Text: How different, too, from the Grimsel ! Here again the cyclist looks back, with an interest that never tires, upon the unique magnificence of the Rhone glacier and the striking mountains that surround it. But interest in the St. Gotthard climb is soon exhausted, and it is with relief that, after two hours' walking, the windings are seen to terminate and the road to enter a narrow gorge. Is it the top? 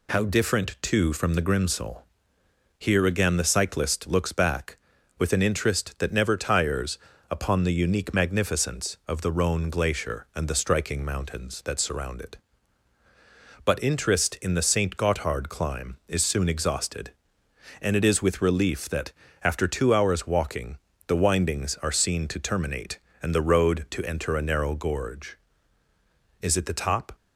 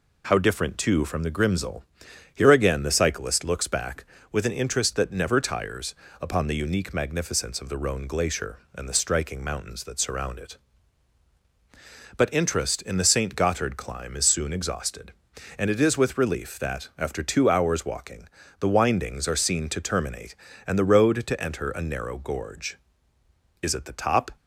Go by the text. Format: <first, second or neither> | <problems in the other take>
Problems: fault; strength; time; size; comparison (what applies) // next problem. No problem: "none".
neither | none